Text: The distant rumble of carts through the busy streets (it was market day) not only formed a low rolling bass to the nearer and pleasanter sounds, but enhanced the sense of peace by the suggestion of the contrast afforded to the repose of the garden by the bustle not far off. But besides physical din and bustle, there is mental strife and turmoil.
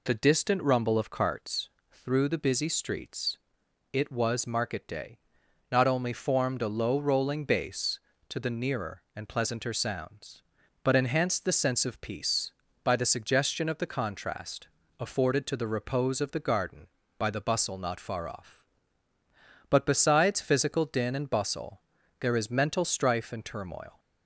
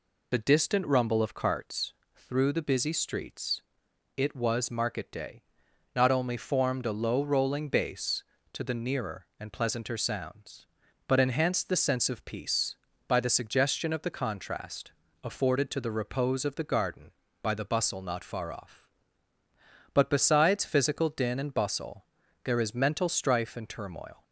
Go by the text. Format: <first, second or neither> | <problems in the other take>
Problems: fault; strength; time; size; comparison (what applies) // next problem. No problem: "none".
first | loses the start of "The"; at 0.3 s; 20 ms // pauses between "carts" and "through"; slight; at 1.9 s; 0.24 s long; slight in the first // pauses between "contrast" and "afforded"; slight; at 14.9 s; 0.28 s long; slight in the first